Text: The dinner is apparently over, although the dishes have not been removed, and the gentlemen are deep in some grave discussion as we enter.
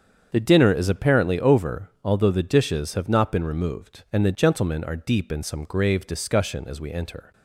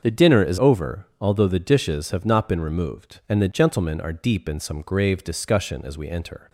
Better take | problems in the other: first | starts louder than the rest; until 1.0 s; 6.5 dB; strong in the first // skips "apparently"; at 0.5 s

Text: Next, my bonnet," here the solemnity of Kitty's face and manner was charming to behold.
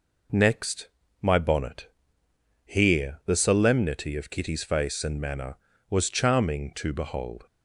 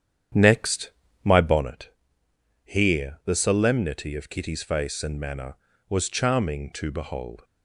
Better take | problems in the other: first | starts louder than the rest; strong; until 1.7 s; 9 dB

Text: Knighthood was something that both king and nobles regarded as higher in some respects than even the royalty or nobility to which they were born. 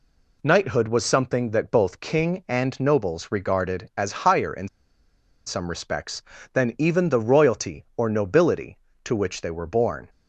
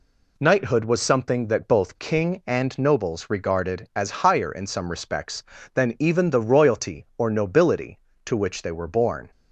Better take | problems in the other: second | pauses between "in" and "some"; noticeable; at 4.6 s; 0.77 s long

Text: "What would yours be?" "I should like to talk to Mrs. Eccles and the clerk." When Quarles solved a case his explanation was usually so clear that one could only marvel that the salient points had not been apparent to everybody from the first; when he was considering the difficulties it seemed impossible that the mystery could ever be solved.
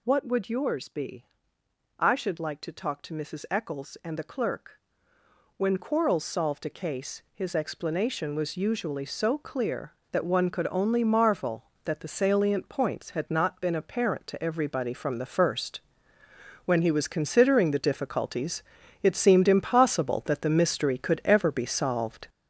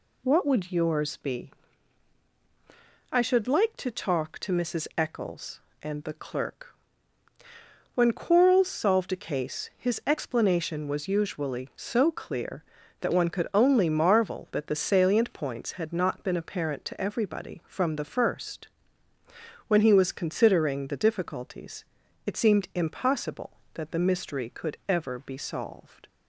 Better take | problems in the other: second | gets louder; throughout; 6.5 dB // pauses between "difficulties" and "it"; at 18.6 s; 0.40 s long; also in the second

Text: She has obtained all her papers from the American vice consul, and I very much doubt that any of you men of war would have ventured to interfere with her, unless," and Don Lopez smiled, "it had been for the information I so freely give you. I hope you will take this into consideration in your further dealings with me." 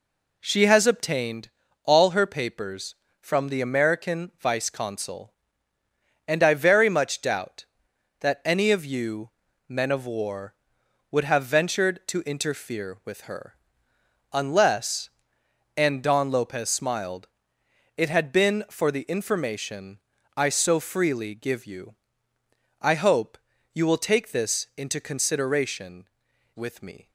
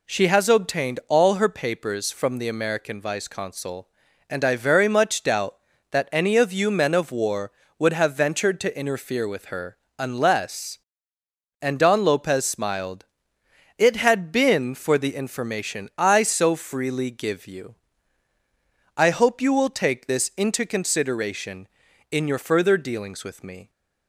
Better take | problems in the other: second | pauses between "obtained" and "all"; slight; at 1.4 s; 0.36 s long // pauses between "you" and "men"; slight; at 9.3 s; 0.36 s long // pauses between "information" and "I"; at 19.9 s; 0.38 s long // pauses between "hope" and "you"; slight; at 23.3 s; 0.36 s long // skips "in your further dealings"; at 26.3 s

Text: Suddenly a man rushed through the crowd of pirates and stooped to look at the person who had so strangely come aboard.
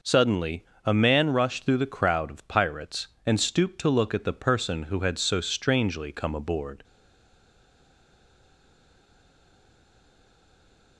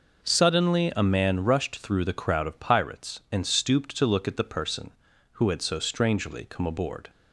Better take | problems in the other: second | pauses between "Suddenly" and "a"; slight; at 0.6 s; 0.18 s long // stays silent after the last word; strong; from 6.8 s on; 4.1 s long

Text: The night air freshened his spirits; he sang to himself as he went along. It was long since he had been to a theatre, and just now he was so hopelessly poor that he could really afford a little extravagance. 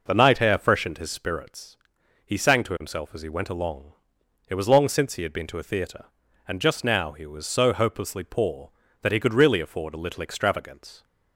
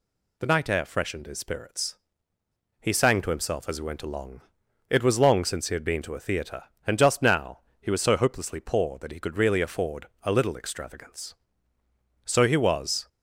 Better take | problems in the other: first | pauses between "now" and "he"; slight; at 7.5 s; 0.20 s long // pauses between "afford" and "a"; slight; at 10.0 s; 0.16 s long // goes on to say "So he was"; noticeable; from 12.2 s on; 0.84 s long

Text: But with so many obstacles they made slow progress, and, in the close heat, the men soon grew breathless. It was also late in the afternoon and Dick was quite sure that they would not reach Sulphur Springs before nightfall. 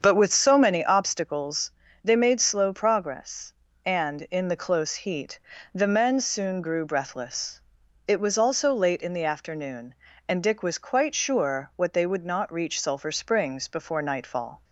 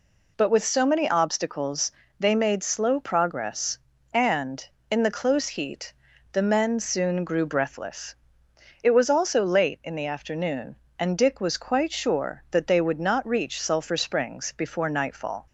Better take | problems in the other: second | starts louder than the rest; strong; until 1.0 s; 7 dB // pauses between "obstacles" and "they"; slight; at 1.6 s; 0.34 s long; slight in the second // says "what" for "that"; at 11.7 s

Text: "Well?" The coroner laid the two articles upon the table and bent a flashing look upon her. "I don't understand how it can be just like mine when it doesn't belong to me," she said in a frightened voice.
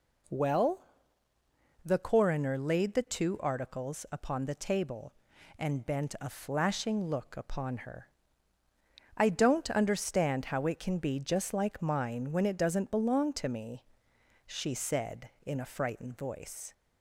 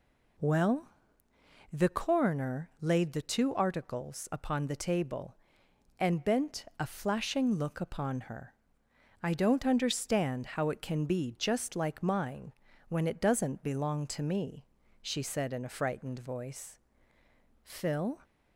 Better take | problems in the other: first | pauses between "mine" and "when"; slight; at 12.5 s; 0.36 s long // goes on to say "Phil"; from 17.6 s on; 0.54 s long

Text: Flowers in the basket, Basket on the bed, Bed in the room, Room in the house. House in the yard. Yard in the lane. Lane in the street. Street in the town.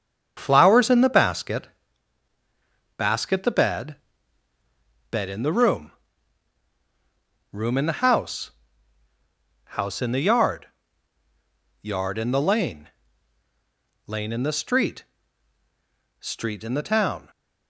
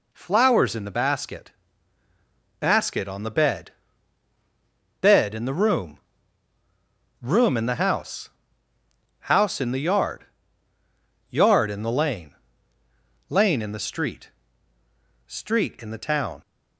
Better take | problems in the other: second | starts louder than the rest; strong; until 1.3 s; 7.5 dB // skips "on"; at 3.4 s

